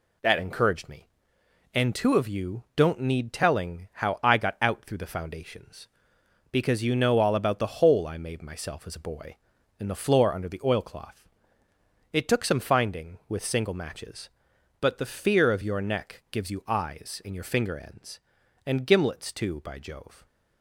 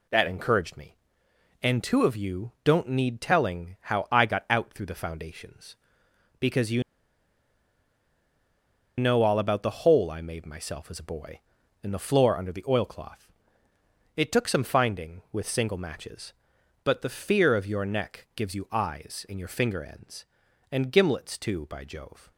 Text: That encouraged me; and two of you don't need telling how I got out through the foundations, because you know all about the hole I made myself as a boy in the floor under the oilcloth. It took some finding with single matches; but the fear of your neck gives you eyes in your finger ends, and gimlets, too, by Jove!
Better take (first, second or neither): first